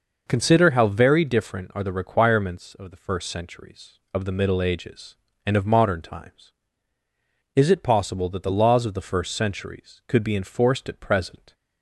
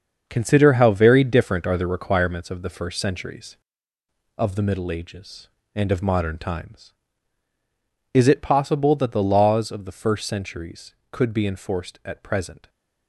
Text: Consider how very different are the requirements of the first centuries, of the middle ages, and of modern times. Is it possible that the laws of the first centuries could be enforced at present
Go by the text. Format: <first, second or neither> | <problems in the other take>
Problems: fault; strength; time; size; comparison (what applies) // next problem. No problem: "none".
first | gets quieter; strong; throughout; 9 dB